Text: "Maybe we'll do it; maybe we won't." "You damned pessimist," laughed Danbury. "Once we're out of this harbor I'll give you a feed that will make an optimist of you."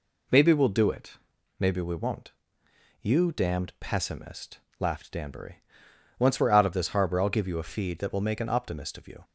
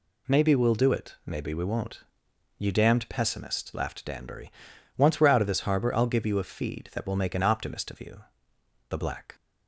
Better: first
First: none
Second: goes on to say "The black"; slight; from 8.8 s on; 0.46 s long

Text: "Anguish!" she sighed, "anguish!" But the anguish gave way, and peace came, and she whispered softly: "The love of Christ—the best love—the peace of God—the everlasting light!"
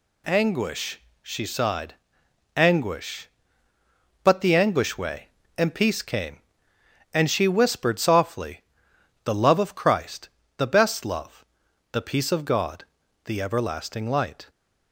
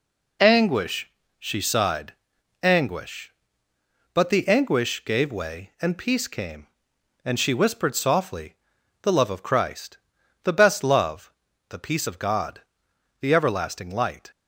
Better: second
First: skips "gave"; at 4.9 s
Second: none

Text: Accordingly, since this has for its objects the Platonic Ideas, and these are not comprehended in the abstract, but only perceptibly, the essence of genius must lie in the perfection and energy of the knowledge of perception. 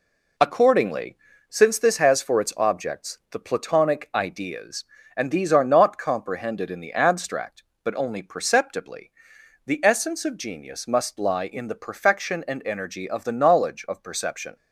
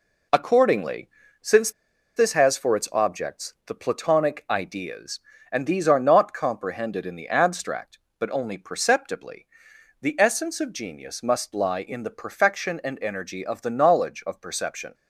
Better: first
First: none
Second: pauses between "since" and "this"; at 1.7 s; 0.45 s long

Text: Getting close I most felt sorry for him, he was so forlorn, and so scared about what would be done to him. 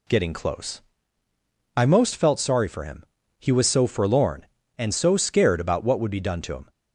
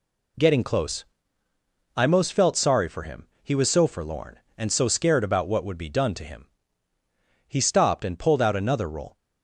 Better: first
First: pauses between "close" and "I"; noticeable; at 0.7 s; 0.96 s long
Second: pauses between "close" and "I"; noticeable; at 1.0 s; 0.90 s long // goes on to say "He stopped and pulled out another roll"; strong; from 7.4 s on; 1.7 s long

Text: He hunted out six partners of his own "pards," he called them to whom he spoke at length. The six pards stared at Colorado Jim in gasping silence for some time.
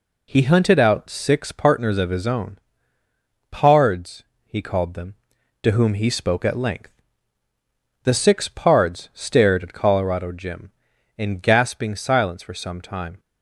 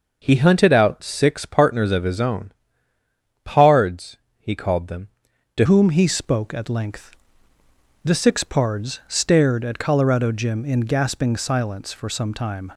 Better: first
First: pauses between "own" and "pards"; noticeable; at 2.5 s; 0.92 s long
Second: pauses between "own" and "pards"; noticeable; at 2.5 s; 0.92 s long // changes voice at "whom"; from 5.6 s on; 7.1 s long

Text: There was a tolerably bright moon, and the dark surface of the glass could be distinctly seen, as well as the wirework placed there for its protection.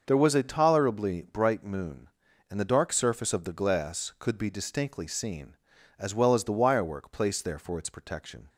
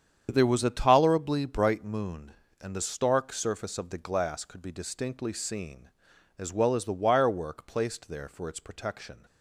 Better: first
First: starts louder than the rest; noticeable; until 1.0 s; 6 dB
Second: starts louder than the rest; strong; until 1.3 s; 8 dB // says "stark" for "dark"; at 2.8 s

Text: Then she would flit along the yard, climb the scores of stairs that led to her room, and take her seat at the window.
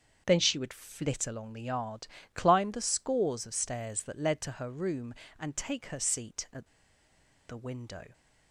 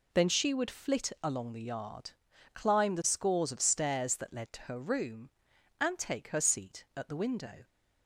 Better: second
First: starts louder than the rest; until 1.2 s; 6.5 dB // pauses between "at" and "the"; noticeable; at 6.6 s; 0.80 s long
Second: none

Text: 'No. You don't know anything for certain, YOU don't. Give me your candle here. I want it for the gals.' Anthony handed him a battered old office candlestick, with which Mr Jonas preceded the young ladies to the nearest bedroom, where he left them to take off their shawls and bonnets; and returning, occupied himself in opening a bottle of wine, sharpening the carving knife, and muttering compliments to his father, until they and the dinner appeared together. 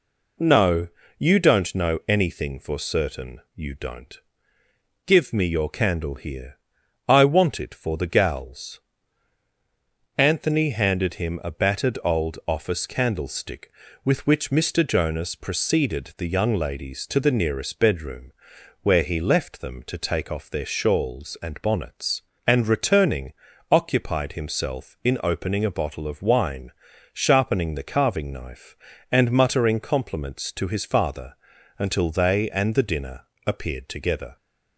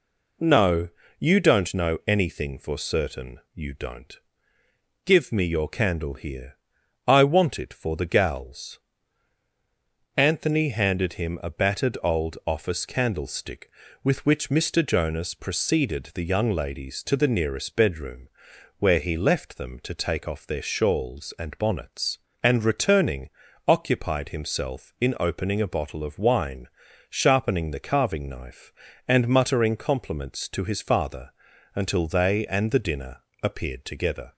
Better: neither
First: pauses between "dinner" and "appeared"; slight; at 33.2 s; 0.24 s long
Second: pauses between "dinner" and "appeared"; slight; at 33.1 s; 0.24 s long

